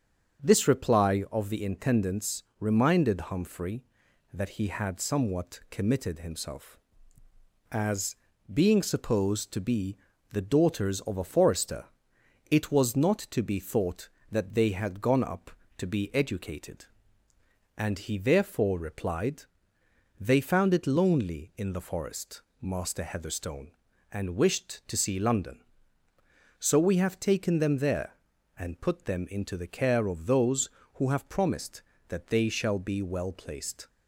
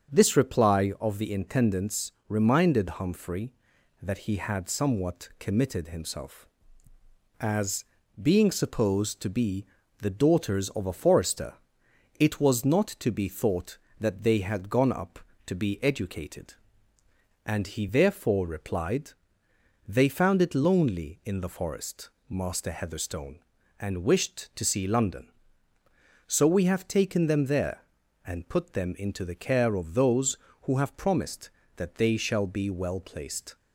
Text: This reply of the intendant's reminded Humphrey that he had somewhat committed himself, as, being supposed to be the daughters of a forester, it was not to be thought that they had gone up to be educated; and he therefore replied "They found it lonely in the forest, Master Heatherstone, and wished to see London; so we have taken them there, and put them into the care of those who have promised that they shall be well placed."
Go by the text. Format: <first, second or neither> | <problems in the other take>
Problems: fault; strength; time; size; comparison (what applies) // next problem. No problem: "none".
neither | starts louder than the rest; the same in both // pauses between "intendant's" and "reminded"; slight; the same in both // pauses between "be" and "the"; slight; the same in both // pauses between "replied" and "They"; noticeable; the same in both